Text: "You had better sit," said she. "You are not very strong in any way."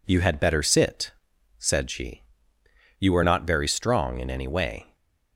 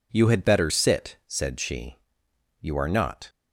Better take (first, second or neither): first